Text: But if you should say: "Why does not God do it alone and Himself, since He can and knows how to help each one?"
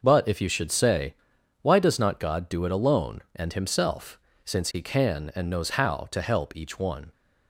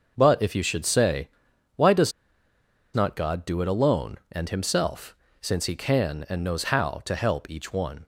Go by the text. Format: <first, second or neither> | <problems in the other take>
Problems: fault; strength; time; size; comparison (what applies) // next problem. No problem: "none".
first | pauses between "does" and "not"; noticeable; at 2.1 s; 0.83 s long